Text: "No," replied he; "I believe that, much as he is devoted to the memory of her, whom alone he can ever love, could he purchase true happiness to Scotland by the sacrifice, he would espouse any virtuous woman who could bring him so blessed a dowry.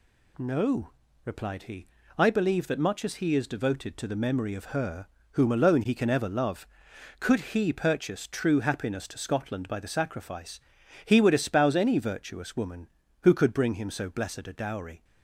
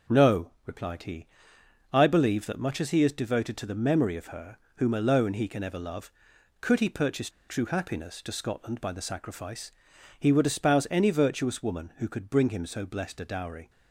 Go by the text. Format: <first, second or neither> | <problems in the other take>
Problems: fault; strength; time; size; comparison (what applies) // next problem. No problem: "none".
first | pauses between "purchase" and "true"; slight; at 7.2 s; 0.19 s long